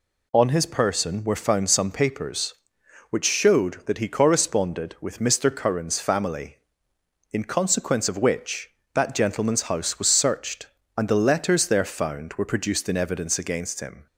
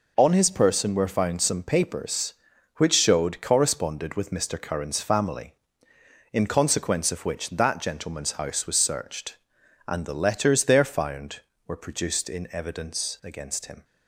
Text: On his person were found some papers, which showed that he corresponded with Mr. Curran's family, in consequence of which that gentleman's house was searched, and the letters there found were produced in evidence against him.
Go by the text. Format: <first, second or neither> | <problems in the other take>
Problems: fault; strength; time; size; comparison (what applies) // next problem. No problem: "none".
first | skips "that he"; at 3.4 s